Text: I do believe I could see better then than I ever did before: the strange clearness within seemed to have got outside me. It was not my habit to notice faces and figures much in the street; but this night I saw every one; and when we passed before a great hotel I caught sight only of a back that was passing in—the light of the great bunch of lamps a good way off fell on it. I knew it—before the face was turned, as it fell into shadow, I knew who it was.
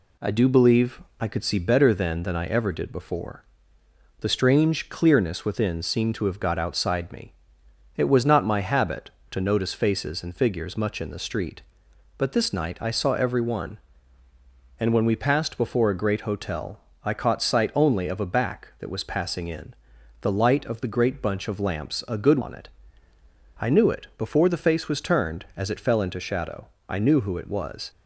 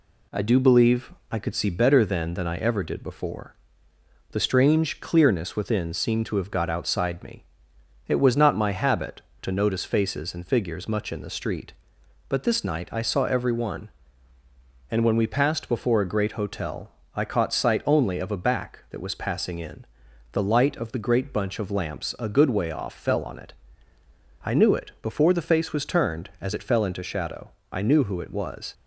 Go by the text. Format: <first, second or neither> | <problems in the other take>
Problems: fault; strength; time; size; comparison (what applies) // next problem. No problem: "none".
second | pauses between "believe" and "I"; slight; at 1.0 s; 0.18 s long; slight in the second // pauses between "hotel" and "I"; slight; at 16.7 s; 0.26 s long; slight in the second // skips "way off fell"; at 22.4 s